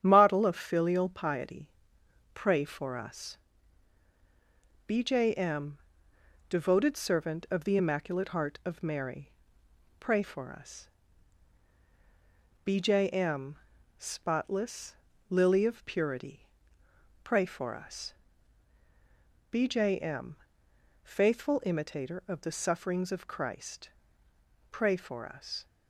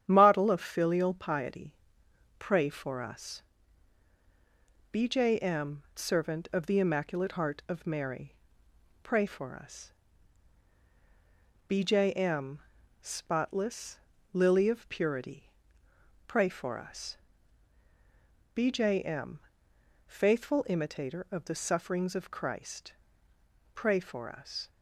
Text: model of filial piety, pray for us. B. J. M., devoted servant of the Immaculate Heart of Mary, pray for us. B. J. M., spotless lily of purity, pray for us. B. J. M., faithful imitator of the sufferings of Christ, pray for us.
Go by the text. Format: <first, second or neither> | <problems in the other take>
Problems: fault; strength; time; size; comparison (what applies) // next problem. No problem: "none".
first | starts louder than the rest; strong; until 1.0 s; 9.5 dB; strong in the first // skips "devoted"; at 5.9 s // pauses between "spotless" and "lily"; slight; at 13.9 s; 0.34 s long; slight in the first